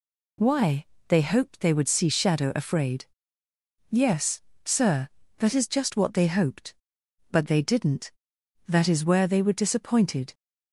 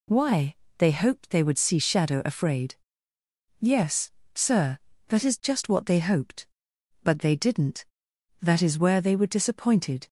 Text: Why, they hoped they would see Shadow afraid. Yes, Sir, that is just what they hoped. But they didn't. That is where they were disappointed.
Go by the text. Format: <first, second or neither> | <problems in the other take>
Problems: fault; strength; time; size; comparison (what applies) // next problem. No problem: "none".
neither | none